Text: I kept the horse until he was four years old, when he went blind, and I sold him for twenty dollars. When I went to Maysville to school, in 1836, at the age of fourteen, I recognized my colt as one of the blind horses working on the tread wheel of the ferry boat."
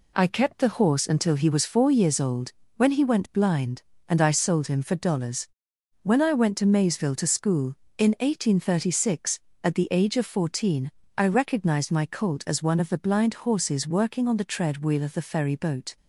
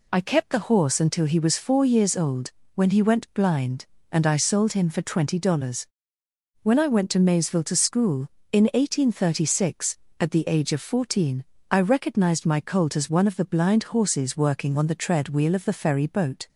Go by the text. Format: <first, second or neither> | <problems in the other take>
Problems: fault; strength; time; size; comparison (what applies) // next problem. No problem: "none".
second | skips "twenty"; at 4.9 s